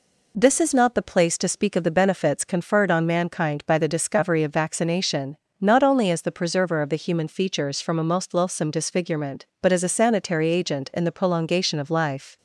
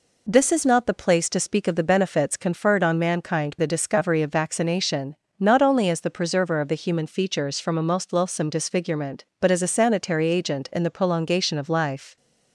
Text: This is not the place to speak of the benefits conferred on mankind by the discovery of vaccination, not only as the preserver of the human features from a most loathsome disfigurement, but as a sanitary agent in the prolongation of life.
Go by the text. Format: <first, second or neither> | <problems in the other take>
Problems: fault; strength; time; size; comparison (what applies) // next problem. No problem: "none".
first | skips "by"; at 3.5 s